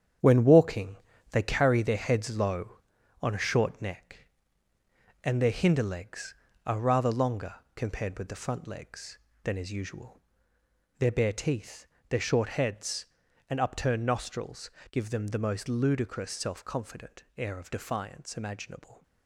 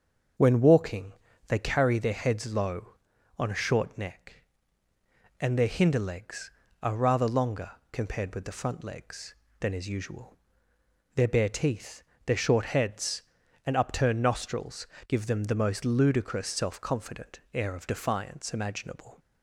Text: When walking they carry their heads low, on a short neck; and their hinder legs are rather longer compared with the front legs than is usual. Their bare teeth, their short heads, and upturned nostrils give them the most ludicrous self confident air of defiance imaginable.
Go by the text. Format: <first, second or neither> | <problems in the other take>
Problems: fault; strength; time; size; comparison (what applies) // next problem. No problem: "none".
second | gets quieter; strong; throughout; 7.5 dB // starts louder than the rest; strong; until 1.5 s; 8.5 dB; also in the second // pauses between "walking" and "they"; slight; at 0.9 s; 0.34 s long; slight in the second // pauses between "longer" and "compared"; slight; at 7.5 s; 0.20 s long; slight in the second // pauses between "nostrils" and "give"; slight; at 14.6 s; 0.22 s long; slight in the second // pauses between "confident" and "air"; slight; at 17.2 s; 0.16 s long; slight in the second